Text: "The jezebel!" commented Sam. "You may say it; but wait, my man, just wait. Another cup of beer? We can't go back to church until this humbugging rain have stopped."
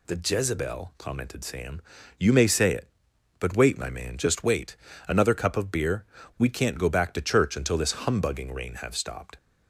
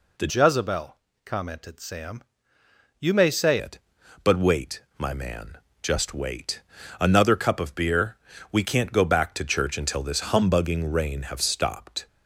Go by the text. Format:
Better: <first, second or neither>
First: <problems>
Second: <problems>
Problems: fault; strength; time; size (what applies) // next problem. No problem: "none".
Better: first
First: none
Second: changes voice from "jezebel" to "say"; from 0.2 to 3.5 s; 3.3 s long